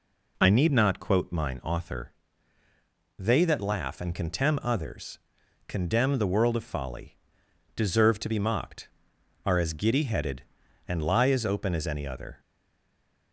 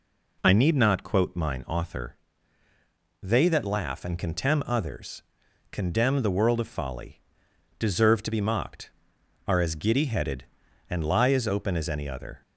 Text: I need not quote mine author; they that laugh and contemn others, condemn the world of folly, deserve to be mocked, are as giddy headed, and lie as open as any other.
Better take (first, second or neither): second